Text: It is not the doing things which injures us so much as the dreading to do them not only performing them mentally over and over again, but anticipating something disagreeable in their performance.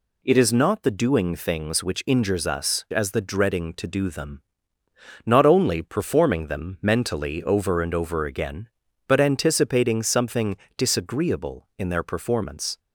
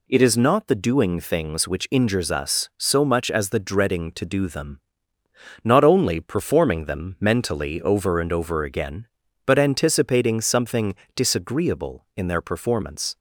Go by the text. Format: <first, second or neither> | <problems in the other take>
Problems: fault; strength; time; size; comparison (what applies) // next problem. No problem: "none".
second | skips "so much"; at 2.8 s // pauses between "them" and "not"; noticeable; at 4.4 s; 0.82 s long; noticeable in the second // pauses between "something" and "disagreeable"; slight; at 10.5 s; 0.20 s long; slight in the second